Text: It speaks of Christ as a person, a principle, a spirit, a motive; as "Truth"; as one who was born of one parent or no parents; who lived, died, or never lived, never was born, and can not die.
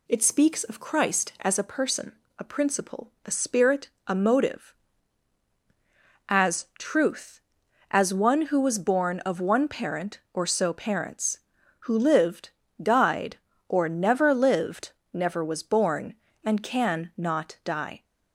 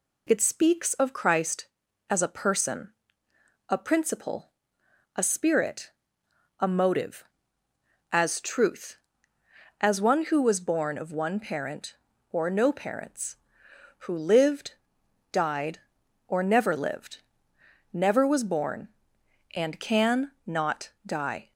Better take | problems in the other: second | says "so" for "no"; at 10.4 s

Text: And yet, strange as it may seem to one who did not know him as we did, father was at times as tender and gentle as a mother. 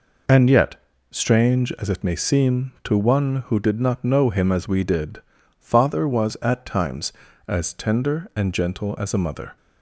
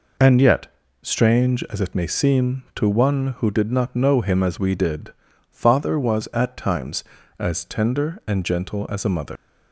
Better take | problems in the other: first | leaves "mother" unfinished; at 9.3 s; 120 ms

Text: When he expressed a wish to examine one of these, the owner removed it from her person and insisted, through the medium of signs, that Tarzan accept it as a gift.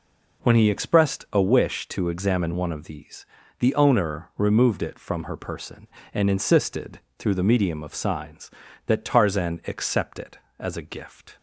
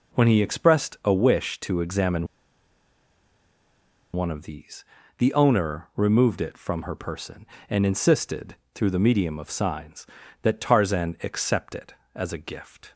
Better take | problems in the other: first | pauses between "examine" and "one"; strong; at 2.2 s; 1.8 s long

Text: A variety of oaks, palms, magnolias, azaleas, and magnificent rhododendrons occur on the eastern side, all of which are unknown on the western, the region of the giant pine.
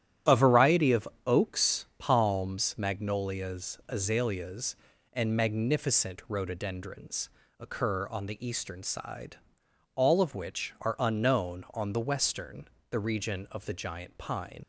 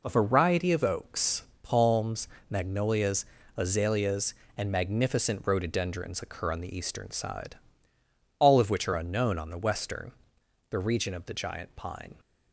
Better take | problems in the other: second | starts louder than the rest; strong; until 1.4 s; 10.5 dB // pauses between "of" and "oaks"; slight; at 1.0 s; 0.18 s long // pauses between "rhododendrons" and "occur"; slight; at 7.2 s; 0.32 s long // leaves "pine" unfinished; at 14.6 s; 50 ms

